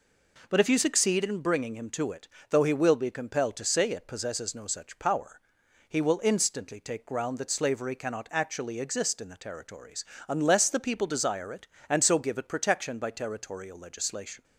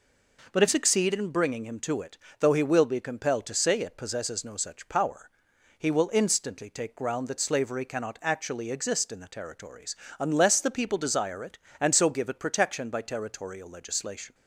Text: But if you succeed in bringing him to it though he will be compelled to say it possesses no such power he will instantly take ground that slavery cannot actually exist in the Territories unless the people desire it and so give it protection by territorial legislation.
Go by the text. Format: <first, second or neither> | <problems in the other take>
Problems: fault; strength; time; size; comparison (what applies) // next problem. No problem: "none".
first | skips "you"; at 0.6 s // pauses between "it" and "though"; slight; at 2.1 s; 0.24 s long; slight in the first // pauses between "power" and "he"; noticeable; at 5.3 s; 0.48 s long; noticeable in the first // pauses between "Territories" and "unless"; slight; at 9.9 s; 0.24 s long; slight in the first